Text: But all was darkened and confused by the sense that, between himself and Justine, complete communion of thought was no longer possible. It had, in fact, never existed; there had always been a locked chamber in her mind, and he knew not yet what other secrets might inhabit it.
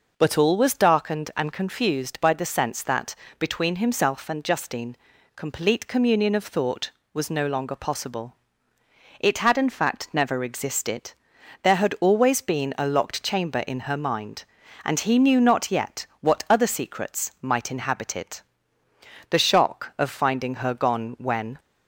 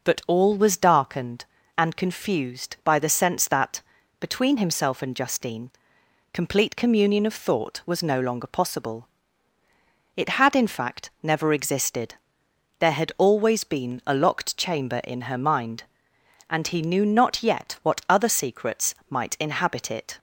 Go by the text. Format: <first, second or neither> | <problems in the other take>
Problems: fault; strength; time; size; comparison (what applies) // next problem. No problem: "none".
second | goes on to say "The shock of finding her gone when"; strong; from 19.3 s on; 2.2 s long